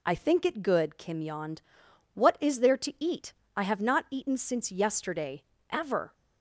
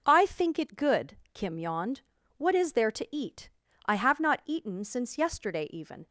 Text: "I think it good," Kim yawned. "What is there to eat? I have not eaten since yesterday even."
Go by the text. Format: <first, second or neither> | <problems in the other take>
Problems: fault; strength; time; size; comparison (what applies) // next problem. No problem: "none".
second | says "ever" for "even"; at 5.6 s